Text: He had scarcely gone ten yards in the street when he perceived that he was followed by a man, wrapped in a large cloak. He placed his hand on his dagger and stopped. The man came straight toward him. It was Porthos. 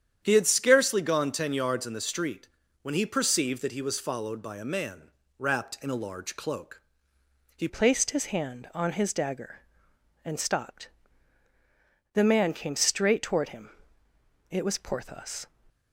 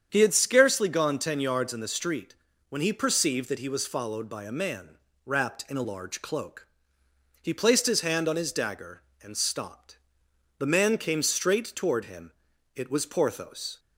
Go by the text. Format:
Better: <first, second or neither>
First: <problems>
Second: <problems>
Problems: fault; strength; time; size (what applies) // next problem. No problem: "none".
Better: second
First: starts louder than the rest; strong; until 1.2 s; 9 dB // pauses between "street" and "when"; slight; at 2.4 s; 0.34 s long // changes voice at "placed"; from 7.6 s on; 7.8 s long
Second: starts louder than the rest; strong; until 1.1 s; 8 dB // pauses between "street" and "when"; slight; at 2.3 s; 0.34 s long